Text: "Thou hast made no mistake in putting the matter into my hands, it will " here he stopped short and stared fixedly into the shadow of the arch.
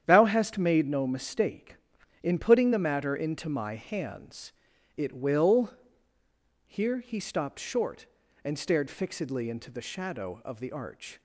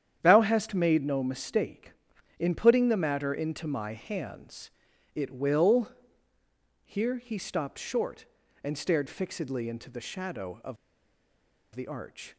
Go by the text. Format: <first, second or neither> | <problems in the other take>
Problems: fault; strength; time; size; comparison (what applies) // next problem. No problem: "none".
first | starts louder than the rest; strong; until 1.2 s; 9.5 dB; strong in the first // pauses between "of" and "the"; noticeable; at 10.7 s; 0.97 s long